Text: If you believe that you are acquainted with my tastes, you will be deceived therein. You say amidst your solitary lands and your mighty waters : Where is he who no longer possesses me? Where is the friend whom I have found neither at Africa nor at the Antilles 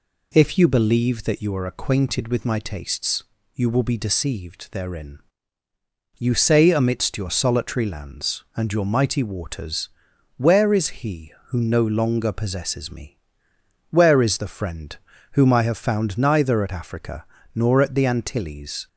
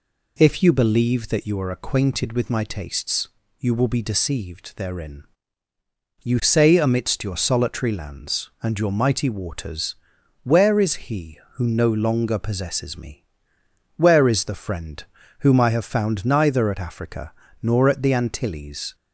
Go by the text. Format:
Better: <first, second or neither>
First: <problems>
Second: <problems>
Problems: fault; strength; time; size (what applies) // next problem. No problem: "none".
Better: neither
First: pauses between "friend" and "whom"; slight; at 14.9 s; 0.36 s long // pauses between "Africa" and "nor"; slight; at 17.2 s; 0.28 s long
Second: pauses between "friend" and "whom"; slight; at 15.0 s; 0.36 s long // pauses between "Africa" and "nor"; slight; at 17.3 s; 0.28 s long